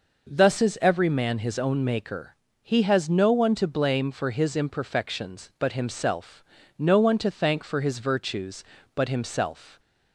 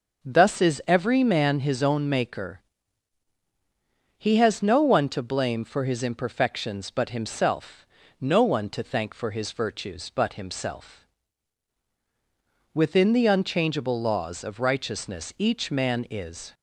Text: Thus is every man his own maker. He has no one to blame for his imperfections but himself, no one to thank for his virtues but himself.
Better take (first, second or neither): first